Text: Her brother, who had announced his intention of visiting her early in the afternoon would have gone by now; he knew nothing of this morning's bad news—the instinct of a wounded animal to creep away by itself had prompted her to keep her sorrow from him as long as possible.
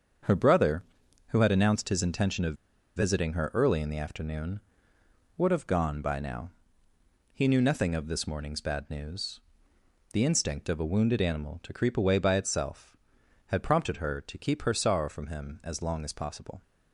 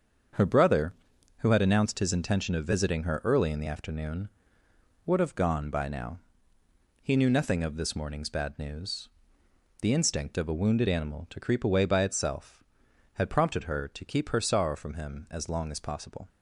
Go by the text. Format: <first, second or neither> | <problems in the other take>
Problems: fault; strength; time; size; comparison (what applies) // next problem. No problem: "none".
second | starts louder than the rest; until 1.6 s; 7 dB; also in the second // pauses between "of" and "visiting"; at 2.5 s; 0.42 s long